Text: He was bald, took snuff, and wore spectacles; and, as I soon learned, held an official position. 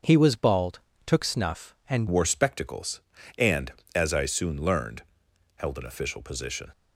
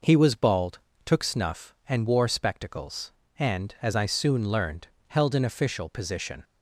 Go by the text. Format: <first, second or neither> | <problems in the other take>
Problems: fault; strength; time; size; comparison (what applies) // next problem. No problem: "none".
second | starts louder than the rest; until 1.3 s; 6.5 dB // changes voice at "wore"; from 2.1 s on; 4.6 s long